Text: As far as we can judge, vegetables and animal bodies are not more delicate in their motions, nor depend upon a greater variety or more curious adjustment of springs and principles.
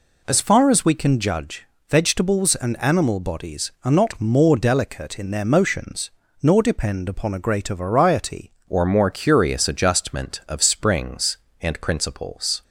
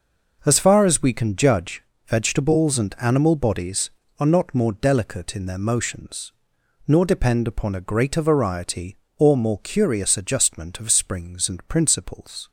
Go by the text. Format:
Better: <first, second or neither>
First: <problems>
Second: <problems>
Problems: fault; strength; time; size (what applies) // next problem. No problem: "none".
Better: second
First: changes voice at "or"; from 8.6 s on; 4.0 s long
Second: none